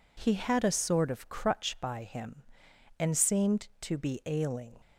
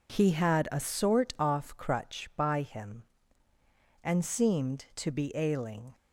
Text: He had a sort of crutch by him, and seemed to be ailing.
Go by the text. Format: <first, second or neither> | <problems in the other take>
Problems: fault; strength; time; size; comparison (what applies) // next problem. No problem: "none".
first | says "off" for "of"; at 1.3 s